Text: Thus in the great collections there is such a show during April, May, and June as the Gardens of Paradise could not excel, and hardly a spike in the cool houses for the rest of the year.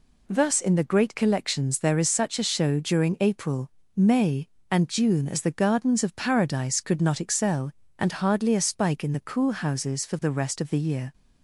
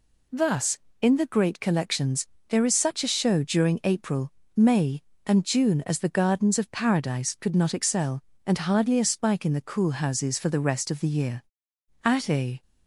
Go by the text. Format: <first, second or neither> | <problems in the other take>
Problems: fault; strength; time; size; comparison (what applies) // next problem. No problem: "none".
first | pauses between "collections" and "there"; slight; at 2.2 s; 0.22 s long // goes on to say "At a"; from 12.0 s on; 0.58 s long